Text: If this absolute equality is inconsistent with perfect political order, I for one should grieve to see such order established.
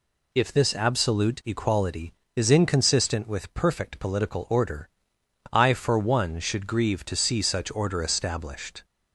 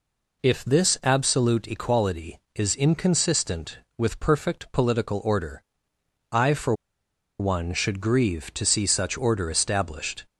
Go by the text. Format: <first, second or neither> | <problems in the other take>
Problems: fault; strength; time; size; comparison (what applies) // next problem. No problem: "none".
first | pauses between "for" and "one"; noticeable; at 6.7 s; 0.66 s long